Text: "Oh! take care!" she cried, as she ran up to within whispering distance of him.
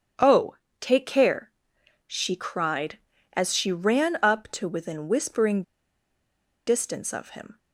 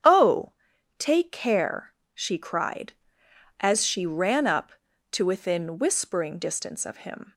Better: second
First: starts louder than the rest; strong; until 1.4 s; 8.5 dB // pauses between "whispering" and "distance"; at 5.6 s; 1.0 s long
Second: starts louder than the rest; strong; until 1.5 s; 8.5 dB

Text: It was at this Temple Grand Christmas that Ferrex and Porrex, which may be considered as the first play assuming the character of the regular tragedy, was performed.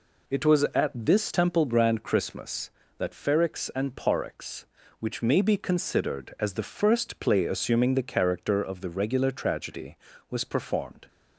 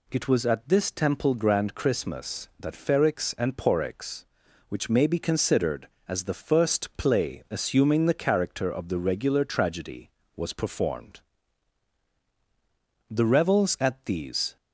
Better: first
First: none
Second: goes on to say "The revels at these"; from 13.1 s on; 1.4 s long

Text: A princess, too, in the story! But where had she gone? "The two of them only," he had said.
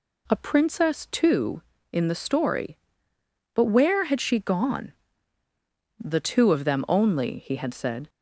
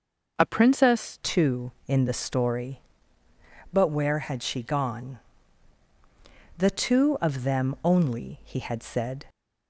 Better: first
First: none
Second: changes voice at "too"; from 1.2 s on; 8.0 s long

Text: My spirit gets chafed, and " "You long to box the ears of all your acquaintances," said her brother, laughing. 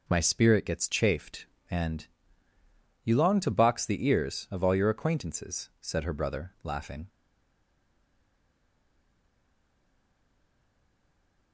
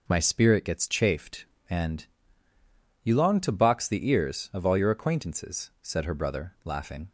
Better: second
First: stays silent after the last word; strong; from 7.0 s on; 4.5 s long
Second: none

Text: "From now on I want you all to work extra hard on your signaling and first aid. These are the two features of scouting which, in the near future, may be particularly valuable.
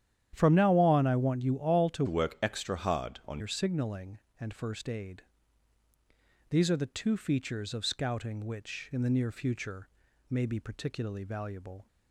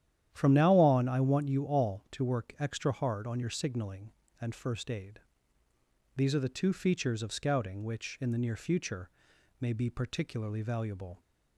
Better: second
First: starts louder than the rest; strong; until 1.3 s; 10 dB // changes voice from "work" to "on"; from 2.0 to 3.4 s; 1.4 s long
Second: starts louder than the rest; strong; until 1.3 s; 10.5 dB

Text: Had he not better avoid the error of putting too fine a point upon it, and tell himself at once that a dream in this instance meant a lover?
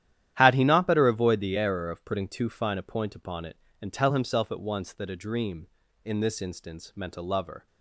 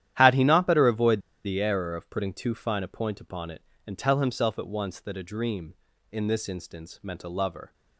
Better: first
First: starts louder than the rest; strong; until 1.4 s; 11.5 dB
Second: starts louder than the rest; strong; until 1.2 s; 11.5 dB // pauses between "avoid" and "the"; slight; at 1.1 s; 0.25 s long

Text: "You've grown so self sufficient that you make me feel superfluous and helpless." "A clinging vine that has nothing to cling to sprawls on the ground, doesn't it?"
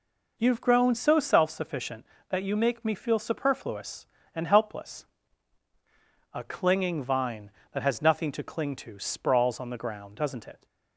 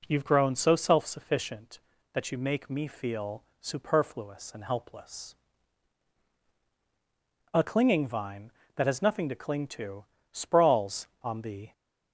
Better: first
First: none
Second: pauses between "feel" and "superfluous"; slight; at 3.4 s; 0.16 s long // pauses between "to" and "sprawls"; slight; at 10.0 s; 0.26 s long // stops before "ground doesn't it"; at 11.7 s

